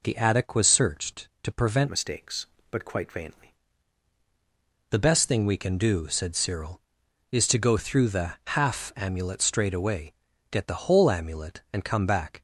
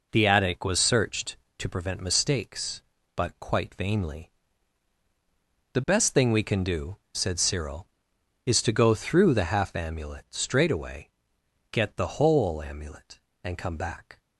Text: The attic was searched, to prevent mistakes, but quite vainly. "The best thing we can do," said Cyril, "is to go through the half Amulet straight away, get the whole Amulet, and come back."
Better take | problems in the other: second | changes voice from "mistakes" to "vainly"; from 1.8 to 3.5 s; 1.7 s long

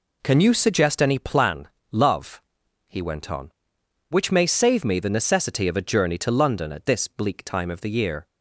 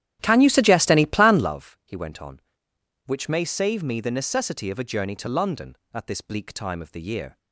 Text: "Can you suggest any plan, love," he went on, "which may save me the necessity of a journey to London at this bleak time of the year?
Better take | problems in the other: first | starts louder than the rest; strong; until 1.5 s; 12 dB

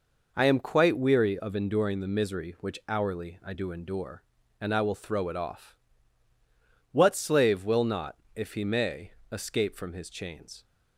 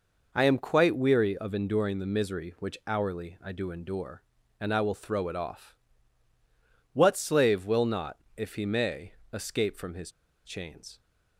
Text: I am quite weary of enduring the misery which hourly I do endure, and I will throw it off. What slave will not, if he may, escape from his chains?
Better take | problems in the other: first | pauses between "his" and "chains"; slight; at 10.1 s; 0.34 s long

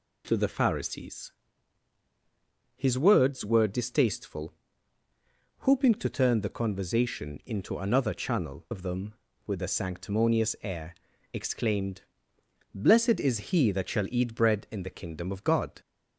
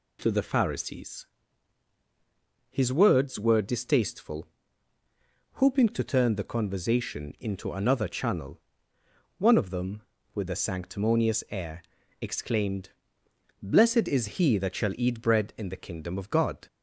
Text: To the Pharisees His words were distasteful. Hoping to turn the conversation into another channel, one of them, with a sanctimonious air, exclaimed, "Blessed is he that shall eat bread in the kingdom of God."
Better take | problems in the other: second | pauses between "Pharisees" and "His"; strong; at 1.2 s; 1.4 s long; strong in the second // skips "one"; at 8.6 s

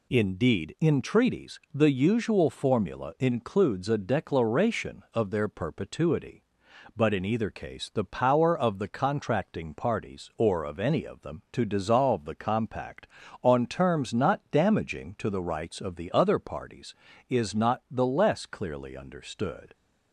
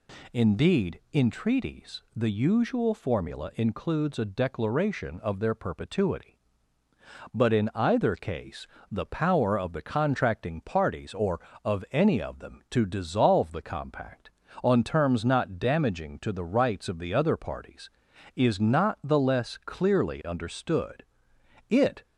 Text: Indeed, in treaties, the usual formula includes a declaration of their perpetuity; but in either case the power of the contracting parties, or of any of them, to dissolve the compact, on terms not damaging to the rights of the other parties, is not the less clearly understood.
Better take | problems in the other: first | pauses between "case" and "the"; slight; at 8.6 s; 0.22 s long // goes on to say "It"; slight; from 21.7 s on; 0.32 s long

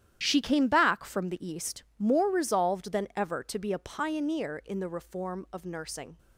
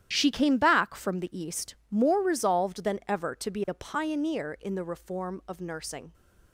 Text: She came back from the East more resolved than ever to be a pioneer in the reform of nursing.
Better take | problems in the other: neither | starts louder than the rest; strong; the same in both // pauses between "East" and "more"; slight; the same in both

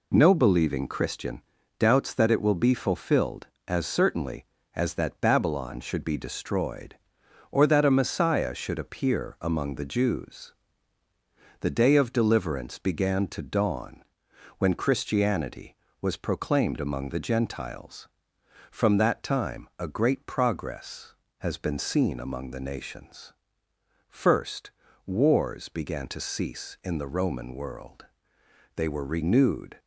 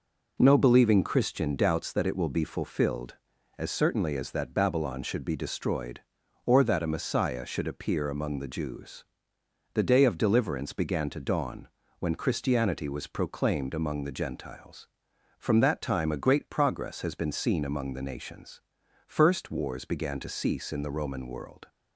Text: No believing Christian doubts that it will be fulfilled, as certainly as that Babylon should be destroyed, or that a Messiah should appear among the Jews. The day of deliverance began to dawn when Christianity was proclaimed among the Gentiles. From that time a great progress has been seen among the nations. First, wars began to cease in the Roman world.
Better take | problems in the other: second | pauses between "Christian" and "doubts"; at 1.4 s; 0.38 s long // pauses between "dawn" and "when"; noticeable; at 14.0 s; 0.56 s long; slight in the second // goes on to say "They were renewed"; noticeable; from 28.7 s on; 1.0 s long

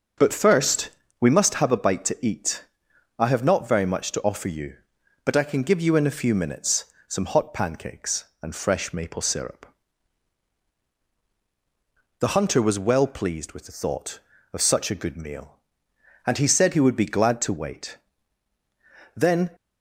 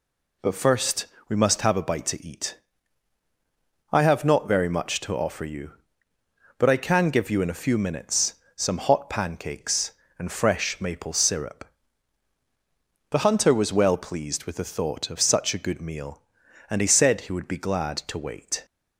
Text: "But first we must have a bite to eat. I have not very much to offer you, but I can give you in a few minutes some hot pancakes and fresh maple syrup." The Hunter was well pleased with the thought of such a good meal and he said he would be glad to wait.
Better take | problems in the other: second | starts louder than the rest; until 1.4 s; 6.5 dB // pauses between "first" and "we"; slight; at 0.9 s; 0.30 s long; slight in the second // pauses between "minutes" and "some"; slight; at 6.8 s; 0.22 s long; slight in the second // goes on to say "Then"; slight; from 19.1 s on; 0.36 s long

